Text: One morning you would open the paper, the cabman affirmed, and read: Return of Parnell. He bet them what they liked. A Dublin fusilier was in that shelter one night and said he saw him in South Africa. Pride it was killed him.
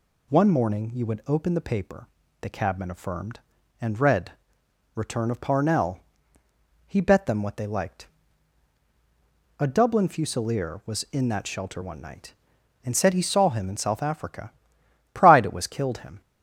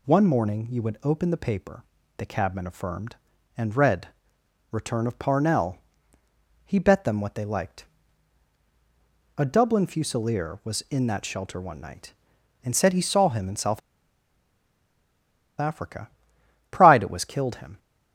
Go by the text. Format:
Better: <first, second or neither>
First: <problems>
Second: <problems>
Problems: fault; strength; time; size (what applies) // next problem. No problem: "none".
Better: first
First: none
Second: pauses between "South" and "Africa"; strong; at 13.8 s; 1.7 s long